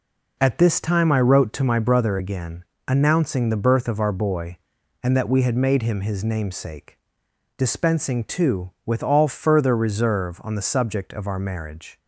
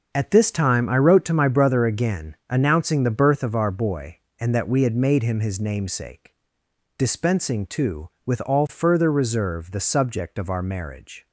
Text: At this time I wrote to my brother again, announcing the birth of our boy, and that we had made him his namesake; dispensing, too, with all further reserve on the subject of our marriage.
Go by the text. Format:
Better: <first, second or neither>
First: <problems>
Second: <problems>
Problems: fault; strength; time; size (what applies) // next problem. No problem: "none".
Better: first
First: none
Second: starts louder than the rest; until 1.1 s; 6.5 dB // skips "on"; at 9.7 s